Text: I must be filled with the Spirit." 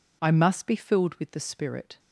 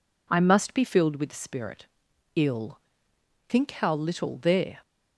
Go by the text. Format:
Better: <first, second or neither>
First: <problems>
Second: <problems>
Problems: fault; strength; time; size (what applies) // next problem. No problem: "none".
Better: first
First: none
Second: goes on to say "Ill Think how little there"; strong; from 2.3 s on; 2.4 s long